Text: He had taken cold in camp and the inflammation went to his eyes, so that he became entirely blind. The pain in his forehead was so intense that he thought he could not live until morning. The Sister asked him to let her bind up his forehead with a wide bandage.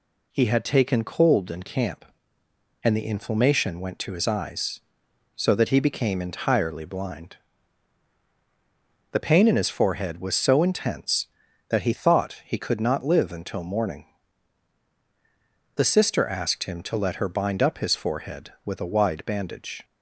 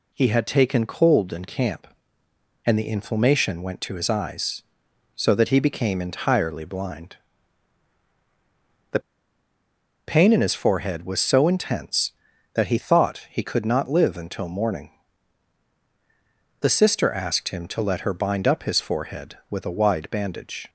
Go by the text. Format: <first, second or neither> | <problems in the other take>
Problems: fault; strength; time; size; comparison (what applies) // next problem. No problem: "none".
first | pauses between "The" and "pain"; at 9.0 s; 1.0 s long